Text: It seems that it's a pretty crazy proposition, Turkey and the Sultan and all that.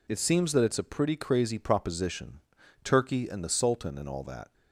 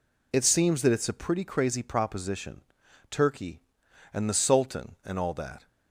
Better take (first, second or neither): neither